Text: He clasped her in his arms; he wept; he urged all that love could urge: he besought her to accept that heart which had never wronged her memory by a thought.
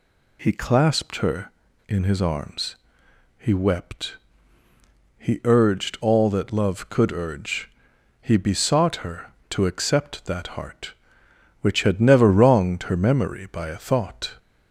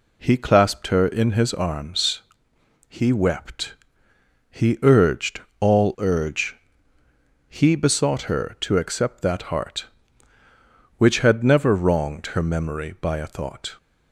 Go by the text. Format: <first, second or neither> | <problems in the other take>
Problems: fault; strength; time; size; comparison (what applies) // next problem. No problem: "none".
first | pauses between "urged" and "all"; slight; at 5.4 s; 0.20 s long // skips "that love could"; at 5.9 s